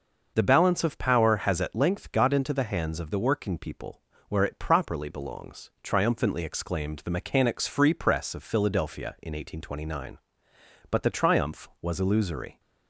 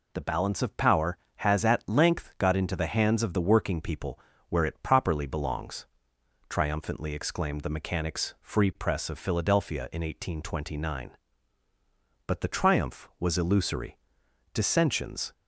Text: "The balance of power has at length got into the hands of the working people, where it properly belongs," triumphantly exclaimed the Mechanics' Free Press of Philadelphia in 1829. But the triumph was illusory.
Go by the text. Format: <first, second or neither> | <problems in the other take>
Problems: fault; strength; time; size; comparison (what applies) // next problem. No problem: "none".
first | goes on to say "Dissensions"; noticeable; from 14.5 s on; 0.80 s long